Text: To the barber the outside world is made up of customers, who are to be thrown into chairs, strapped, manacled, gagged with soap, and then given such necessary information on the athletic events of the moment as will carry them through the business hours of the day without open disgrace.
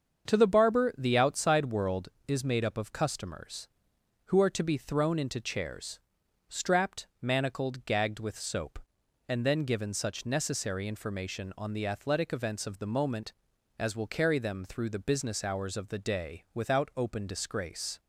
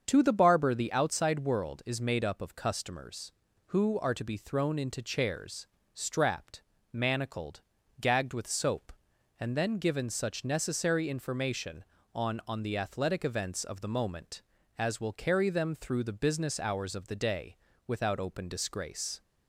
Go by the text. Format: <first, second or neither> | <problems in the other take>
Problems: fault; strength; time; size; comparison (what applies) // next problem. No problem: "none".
first | starts louder than the rest; until 1.0 s; 7 dB; also in the first // says "on" twice; at 12.4 s // pauses between "day" and "without"; slight; at 17.5 s; 0.32 s long